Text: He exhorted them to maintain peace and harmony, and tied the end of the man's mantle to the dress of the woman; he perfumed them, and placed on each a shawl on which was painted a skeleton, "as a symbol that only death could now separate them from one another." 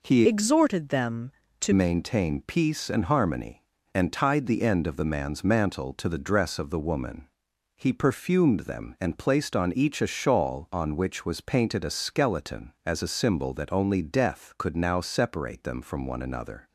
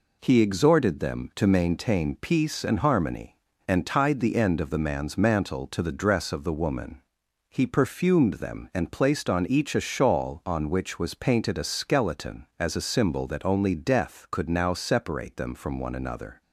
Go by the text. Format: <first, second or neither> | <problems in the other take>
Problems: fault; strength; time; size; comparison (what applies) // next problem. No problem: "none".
second | changes voice from "exhorted" to "to"; from 0.2 to 1.7 s; 1.5 s long